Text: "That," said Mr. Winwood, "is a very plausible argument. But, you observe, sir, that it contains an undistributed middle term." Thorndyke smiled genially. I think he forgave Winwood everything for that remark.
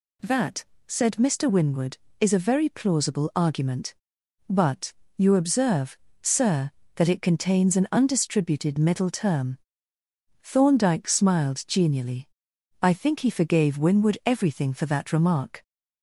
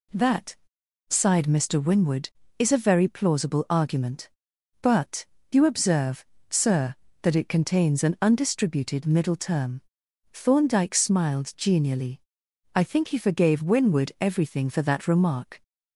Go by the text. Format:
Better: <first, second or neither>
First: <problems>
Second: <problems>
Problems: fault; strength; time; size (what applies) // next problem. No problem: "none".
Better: first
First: none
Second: says "sighed" for "said"; at 1.0 s